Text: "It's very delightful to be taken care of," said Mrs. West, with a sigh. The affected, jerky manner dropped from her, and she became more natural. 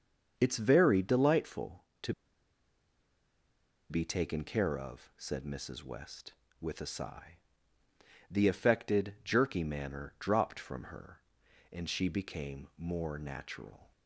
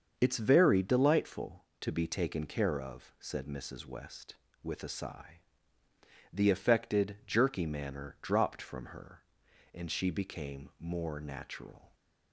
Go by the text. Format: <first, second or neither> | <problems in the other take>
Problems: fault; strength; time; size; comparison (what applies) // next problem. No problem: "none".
second | starts louder than the rest; until 1.3 s; 6.5 dB; also in the second // pauses between "to" and "be"; strong; at 2.1 s; 1.7 s long